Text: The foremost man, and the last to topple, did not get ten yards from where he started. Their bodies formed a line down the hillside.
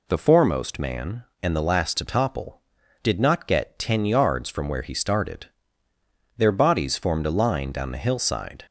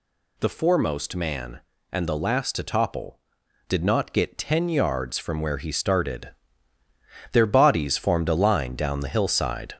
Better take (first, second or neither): first